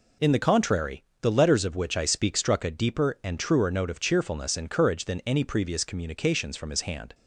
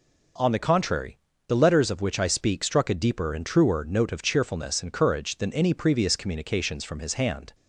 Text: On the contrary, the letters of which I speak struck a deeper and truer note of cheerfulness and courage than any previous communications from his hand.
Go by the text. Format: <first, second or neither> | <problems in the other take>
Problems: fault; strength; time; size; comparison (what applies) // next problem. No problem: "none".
second | says "In" for "On"; at 0.2 s